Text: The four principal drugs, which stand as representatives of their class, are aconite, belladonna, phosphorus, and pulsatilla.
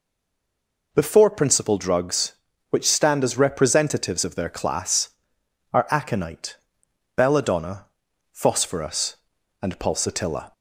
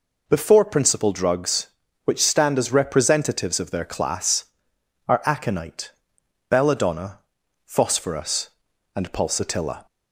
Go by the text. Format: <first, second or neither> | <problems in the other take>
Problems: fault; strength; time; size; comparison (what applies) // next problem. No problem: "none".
second | stays silent before the first word; slight; until 0.9 s; 0.9 s long